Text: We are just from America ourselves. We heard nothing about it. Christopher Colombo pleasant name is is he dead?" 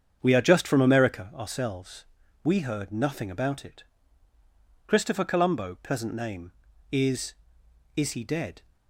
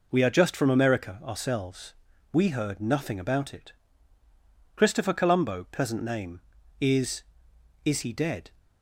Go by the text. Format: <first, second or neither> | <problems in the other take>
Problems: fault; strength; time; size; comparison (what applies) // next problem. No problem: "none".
second | starts louder than the rest; strong; until 1.3 s; 7.5 dB